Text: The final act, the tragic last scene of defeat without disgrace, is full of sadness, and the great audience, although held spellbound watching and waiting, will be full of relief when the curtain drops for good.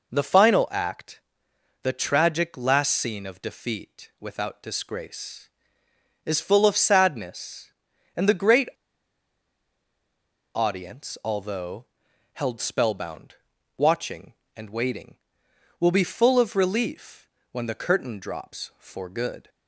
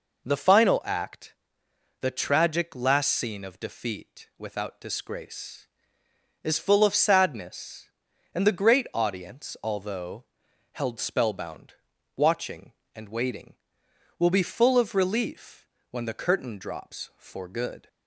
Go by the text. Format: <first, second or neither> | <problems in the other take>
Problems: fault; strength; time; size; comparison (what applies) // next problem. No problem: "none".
second | pauses between "great" and "audience"; strong; at 8.6 s; 1.8 s long // pauses between "although" and "held"; noticeable; at 11.8 s; 0.48 s long; noticeable in the second // pauses between "spellbound" and "watching"; at 13.3 s; 0.42 s long; also in the second // pauses between "relief" and "when"; slight; at 17.2 s; 0.26 s long; slight in the second